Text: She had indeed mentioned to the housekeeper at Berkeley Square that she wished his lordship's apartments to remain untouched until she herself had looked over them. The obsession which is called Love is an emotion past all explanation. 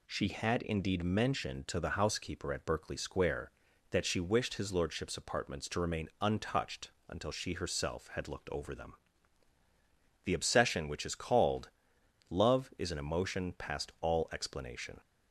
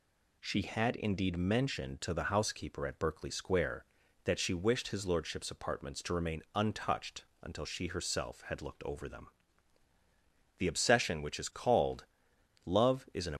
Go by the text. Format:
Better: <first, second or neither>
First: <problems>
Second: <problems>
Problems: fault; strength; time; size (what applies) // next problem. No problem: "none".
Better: first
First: pauses between "untouched" and "until"; slight; at 6.9 s; 0.16 s long // pauses between "called" and "Love"; noticeable; at 11.6 s; 0.60 s long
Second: pauses between "untouched" and "until"; slight; at 7.2 s; 0.16 s long // pauses between "called" and "Love"; noticeable; at 12.0 s; 0.60 s long // stops before "emotion past all explanation"; at 13.3 s